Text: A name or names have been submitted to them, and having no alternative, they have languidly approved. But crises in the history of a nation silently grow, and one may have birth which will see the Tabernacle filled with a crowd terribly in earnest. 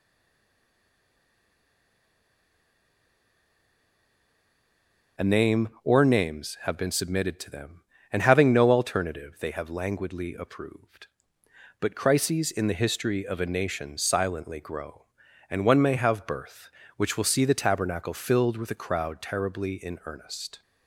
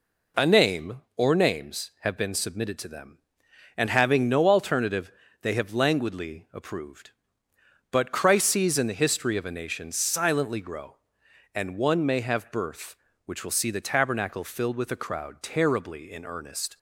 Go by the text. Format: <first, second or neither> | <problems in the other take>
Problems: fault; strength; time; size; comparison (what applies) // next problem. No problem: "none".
second | stays silent before the first word; strong; until 5.1 s; 5.1 s long